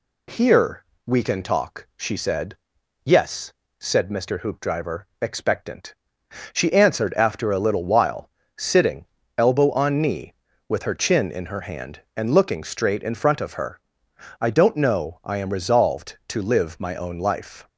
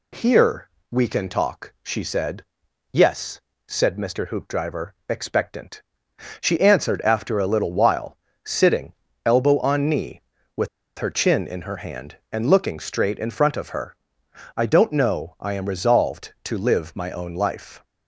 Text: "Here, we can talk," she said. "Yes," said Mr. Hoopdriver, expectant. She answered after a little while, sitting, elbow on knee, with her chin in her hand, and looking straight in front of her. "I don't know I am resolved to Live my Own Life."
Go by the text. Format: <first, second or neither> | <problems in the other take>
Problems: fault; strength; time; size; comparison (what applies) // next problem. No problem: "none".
first | pauses between "with" and "her"; slight; at 10.6 s; 0.29 s long